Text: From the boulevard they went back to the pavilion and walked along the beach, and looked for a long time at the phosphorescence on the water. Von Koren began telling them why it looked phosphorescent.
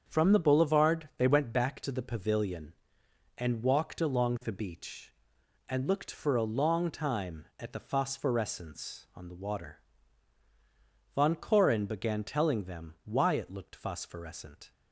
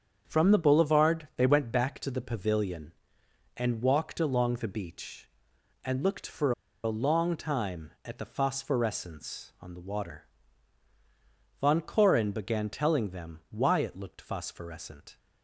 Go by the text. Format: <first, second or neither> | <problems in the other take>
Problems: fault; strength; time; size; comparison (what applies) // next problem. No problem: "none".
first | starts louder than the rest; strong; until 1.2 s; 7 dB; strong in the first // pauses between "for" and "a"; slight; at 6.5 s; 0.33 s long